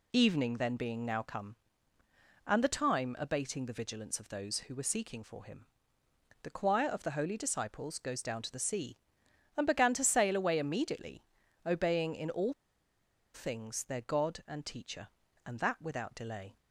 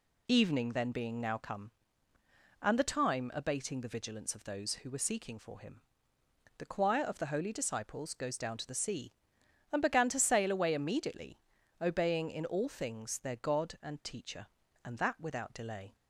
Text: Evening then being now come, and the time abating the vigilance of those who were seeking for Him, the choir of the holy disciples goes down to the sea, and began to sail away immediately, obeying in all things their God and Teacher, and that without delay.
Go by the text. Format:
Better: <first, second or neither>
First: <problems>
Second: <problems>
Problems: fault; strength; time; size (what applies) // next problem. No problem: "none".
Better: second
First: pauses between "all" and "things"; noticeable; at 12.5 s; 0.80 s long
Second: none